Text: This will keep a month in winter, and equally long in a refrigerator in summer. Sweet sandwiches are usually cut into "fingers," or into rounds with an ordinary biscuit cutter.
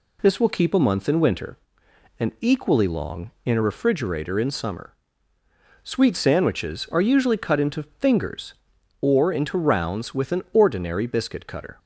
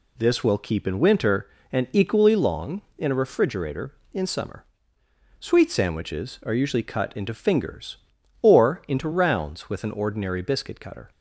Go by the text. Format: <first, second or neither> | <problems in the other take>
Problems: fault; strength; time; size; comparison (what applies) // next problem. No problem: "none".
first | skips "a month"; at 0.8 s